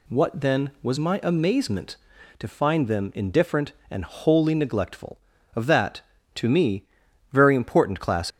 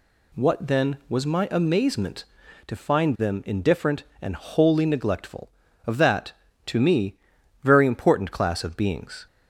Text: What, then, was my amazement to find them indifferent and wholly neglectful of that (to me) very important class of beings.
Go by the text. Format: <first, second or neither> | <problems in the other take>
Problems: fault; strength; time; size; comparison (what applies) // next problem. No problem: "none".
second | stops before "of beings"; at 8.3 s